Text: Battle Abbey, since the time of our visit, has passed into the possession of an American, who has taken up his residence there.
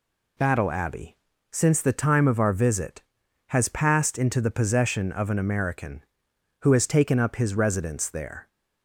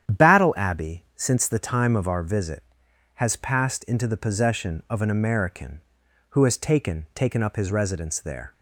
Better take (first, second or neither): first